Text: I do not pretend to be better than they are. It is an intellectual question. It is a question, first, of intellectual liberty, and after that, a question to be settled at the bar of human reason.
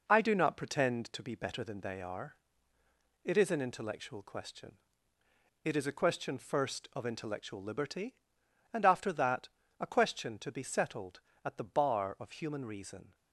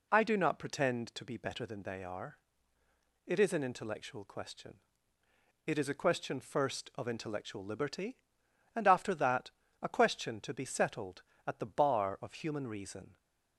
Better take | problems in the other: second | gets quieter; noticeable; throughout; 5.5 dB

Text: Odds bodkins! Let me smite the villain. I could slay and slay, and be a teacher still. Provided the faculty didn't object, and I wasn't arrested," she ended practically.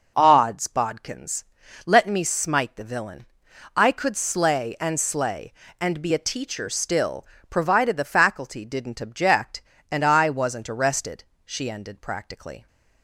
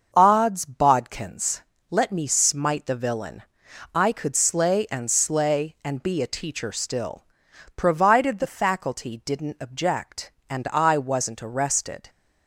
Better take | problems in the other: first | starts louder than the rest; until 1.1 s; 6.5 dB // stops before "she ended practically"; at 12.0 s

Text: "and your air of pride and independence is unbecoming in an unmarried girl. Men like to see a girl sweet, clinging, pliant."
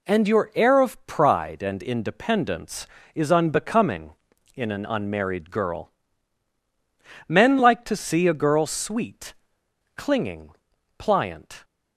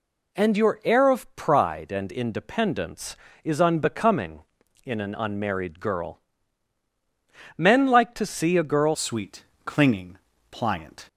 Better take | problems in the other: first | changes voice at "sweet"; from 8.9 s on; 2.1 s long

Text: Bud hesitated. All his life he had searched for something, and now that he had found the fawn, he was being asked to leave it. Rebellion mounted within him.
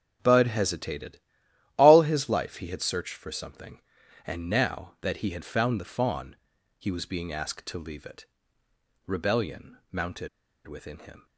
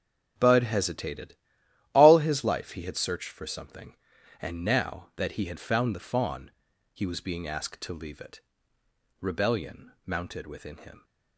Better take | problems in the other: second | starts louder than the rest; until 1.8 s; 6.5 dB; also in the second // pauses between "mounted" and "within"; at 10.2 s; 0.38 s long

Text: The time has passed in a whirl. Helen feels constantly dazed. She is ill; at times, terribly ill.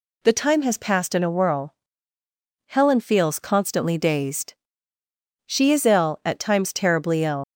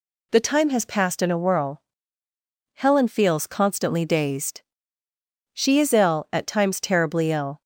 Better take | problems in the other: second | leaves "ill" unfinished; at 7.4 s; 95 ms

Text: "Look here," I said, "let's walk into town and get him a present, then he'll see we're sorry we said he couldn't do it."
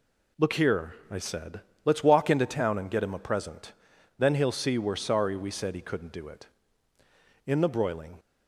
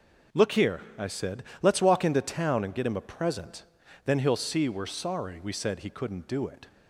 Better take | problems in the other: second | goes on to say "In the broiling"; noticeable; from 7.4 s on; 0.72 s long

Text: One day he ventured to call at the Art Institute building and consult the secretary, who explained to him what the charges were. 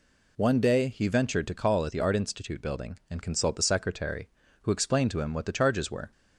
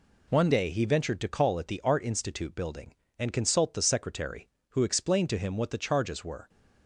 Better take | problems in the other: first | changes voice at "day"; from 0.5 s on; 5.9 s long

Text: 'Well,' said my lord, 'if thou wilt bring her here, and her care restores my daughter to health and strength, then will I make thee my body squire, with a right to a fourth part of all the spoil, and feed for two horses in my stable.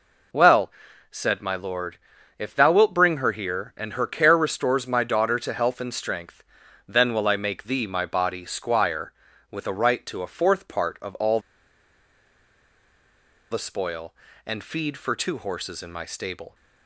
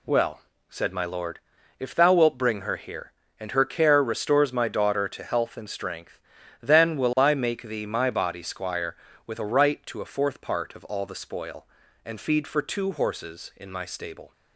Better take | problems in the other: second | pauses between "all" and "the"; strong; at 11.4 s; 2.1 s long

